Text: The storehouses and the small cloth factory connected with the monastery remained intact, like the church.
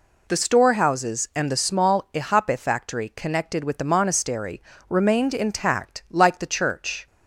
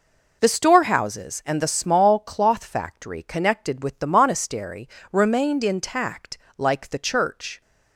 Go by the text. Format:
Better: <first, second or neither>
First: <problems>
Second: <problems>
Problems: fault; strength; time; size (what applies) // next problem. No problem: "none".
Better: second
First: says "ihape" for "cloth"; at 2.1 s // pauses between "monastery" and "remained"; slight; at 4.6 s; 0.28 s long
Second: pauses between "monastery" and "remained"; slight; at 4.8 s; 0.24 s long